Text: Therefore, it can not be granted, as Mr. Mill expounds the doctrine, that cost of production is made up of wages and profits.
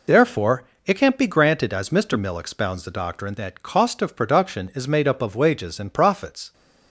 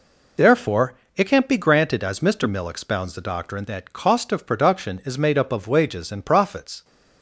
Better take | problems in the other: neither | none

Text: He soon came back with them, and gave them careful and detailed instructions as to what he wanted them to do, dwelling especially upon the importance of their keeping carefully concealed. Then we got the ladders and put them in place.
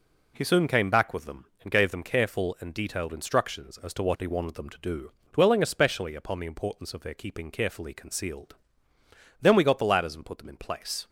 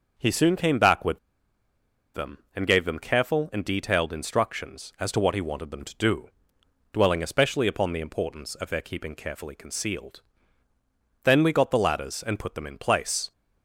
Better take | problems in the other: first | pauses between "with" and "them"; noticeable; at 1.1 s; 0.95 s long

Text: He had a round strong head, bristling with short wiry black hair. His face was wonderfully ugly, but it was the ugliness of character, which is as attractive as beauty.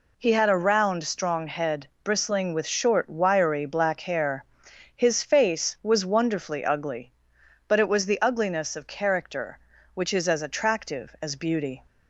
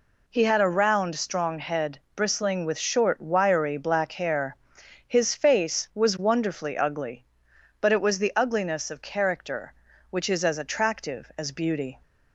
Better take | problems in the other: neither | none

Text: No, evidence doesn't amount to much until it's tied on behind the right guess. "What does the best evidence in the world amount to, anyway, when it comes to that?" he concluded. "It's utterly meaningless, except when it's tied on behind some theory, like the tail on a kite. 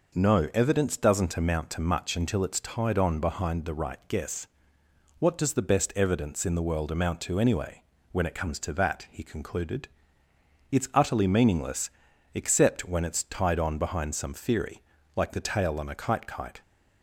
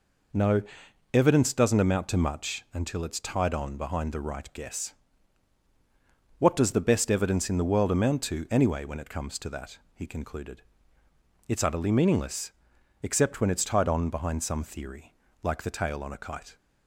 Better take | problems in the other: second | says "kite" twice; at 16.2 s

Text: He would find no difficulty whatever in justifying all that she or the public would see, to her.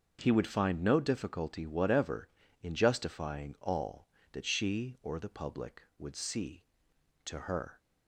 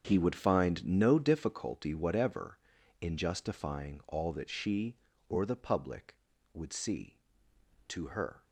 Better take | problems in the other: first | gets quieter; strong; throughout; 14 dB // starts louder than the rest; until 1.0 s; 7 dB; also in the first

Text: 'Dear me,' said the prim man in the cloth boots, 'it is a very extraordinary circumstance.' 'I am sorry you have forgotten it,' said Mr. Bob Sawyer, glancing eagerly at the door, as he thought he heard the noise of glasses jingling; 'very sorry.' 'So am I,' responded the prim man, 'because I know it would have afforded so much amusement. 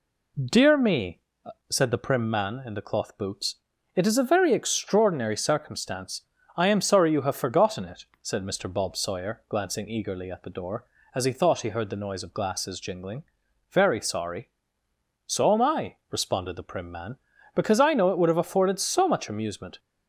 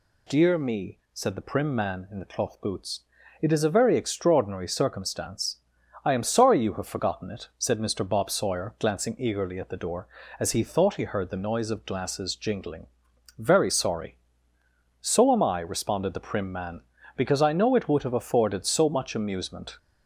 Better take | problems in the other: neither | none

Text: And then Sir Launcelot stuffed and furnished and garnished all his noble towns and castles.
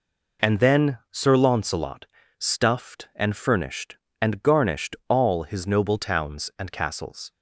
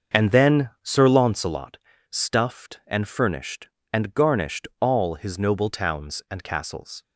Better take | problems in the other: first | starts louder than the rest; until 1.5 s; 6.5 dB // pauses between "Launcelot" and "stuffed"; slight; at 1.7 s; 0.32 s long; slight in the first

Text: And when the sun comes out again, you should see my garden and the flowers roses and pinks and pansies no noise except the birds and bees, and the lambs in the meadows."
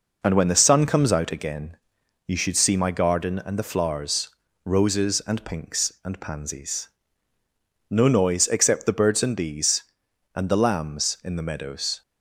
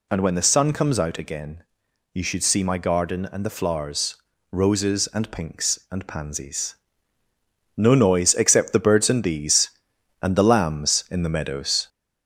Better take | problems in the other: first | gets louder; slight; throughout; 3 dB // pauses between "flowers" and "roses"; slight; at 4.1 s; 0.36 s long; slight in the first // pauses between "pansies" and "no"; at 6.7 s; 1.0 s long; also in the first

